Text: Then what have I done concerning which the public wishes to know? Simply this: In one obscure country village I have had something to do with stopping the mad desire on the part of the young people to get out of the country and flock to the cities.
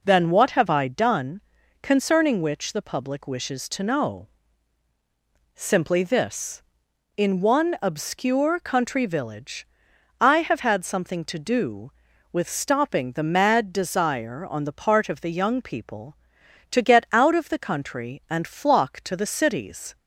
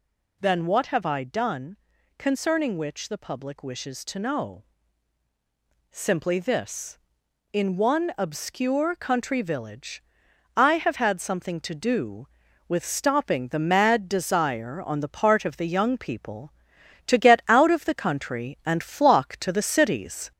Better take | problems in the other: first | gets louder; slight; throughout; 2.5 dB // pauses between "done" and "concerning"; at 1.7 s; 0.42 s long; also in the first // pauses between "village" and "I"; noticeable; at 10.0 s; 0.54 s long; noticeable in the first

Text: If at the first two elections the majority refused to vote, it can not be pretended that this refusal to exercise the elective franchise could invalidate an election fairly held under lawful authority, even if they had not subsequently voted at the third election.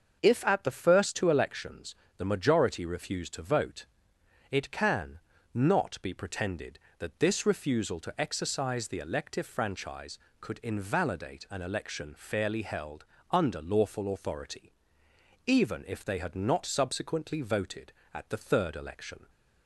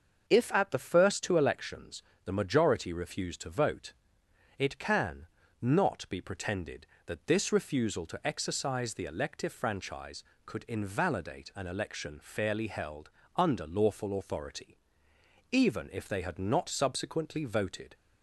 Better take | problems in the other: first | starts louder than the rest; until 1.3 s; 6 dB; also in the first // pauses between "elections" and "the"; slight; at 2.0 s; 0.24 s long; slight in the first // pauses between "can" and "not"; slight; at 5.2 s; 0.34 s long; slight in the first // pauses between "held" and "under"; slight; at 13.1 s; 0.24 s long; slight in the first // stops before "at the third election"; at 17.9 s

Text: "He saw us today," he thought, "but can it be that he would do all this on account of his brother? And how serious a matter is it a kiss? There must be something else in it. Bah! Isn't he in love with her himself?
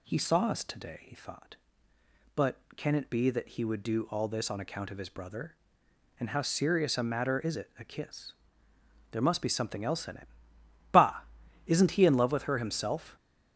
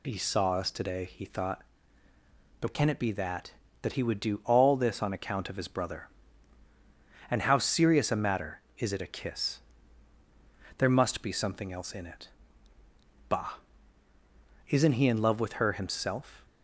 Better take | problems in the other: first | says "that" twice; at 3.8 s

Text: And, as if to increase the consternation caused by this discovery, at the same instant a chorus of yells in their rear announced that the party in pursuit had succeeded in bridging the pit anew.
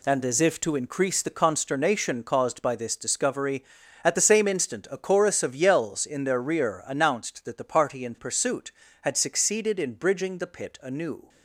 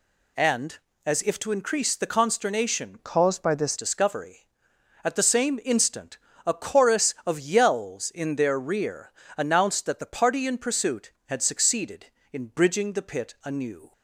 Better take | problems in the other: first | changes voice from "caused" to "this"; from 2.9 to 3.7 s; 0.8 s long // pauses between "instant" and "a"; slight; at 6.1 s; 0.28 s long // pauses between "rear" and "announced"; slight; at 9.0 s; 0.26 s long

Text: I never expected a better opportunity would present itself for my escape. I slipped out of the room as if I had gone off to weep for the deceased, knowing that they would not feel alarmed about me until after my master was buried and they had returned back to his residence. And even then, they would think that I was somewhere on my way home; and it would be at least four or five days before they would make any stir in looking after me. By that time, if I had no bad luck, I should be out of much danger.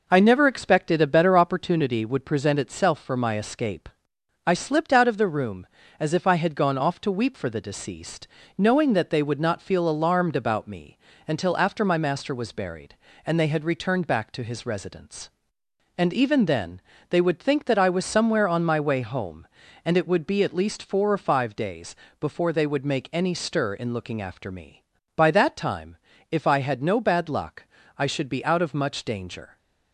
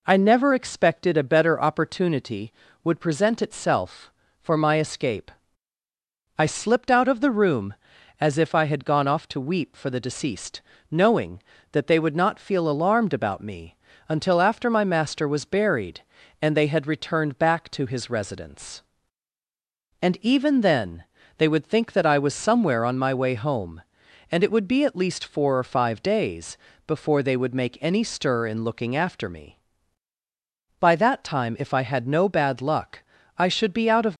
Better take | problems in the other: first | pauses between "me" and "until"; slight; at 13.7 s; 0.32 s long; slight in the first // pauses between "days" and "before"; slight; at 26.5 s; 0.30 s long; slight in the first // stops before "much danger"; at 34.1 s

